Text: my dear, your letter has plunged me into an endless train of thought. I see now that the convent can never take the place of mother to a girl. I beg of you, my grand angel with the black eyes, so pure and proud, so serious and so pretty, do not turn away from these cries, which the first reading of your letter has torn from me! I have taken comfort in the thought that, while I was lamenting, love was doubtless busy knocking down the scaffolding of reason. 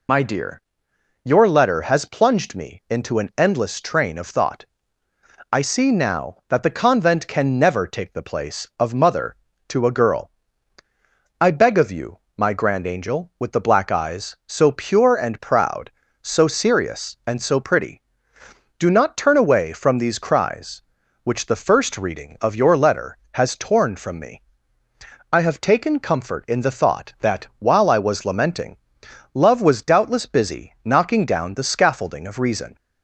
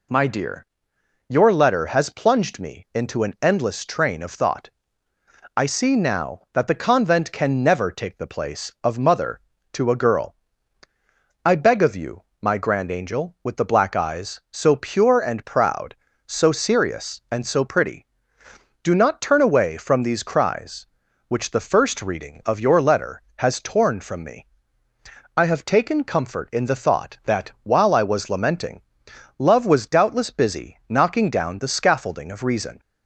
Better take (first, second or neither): second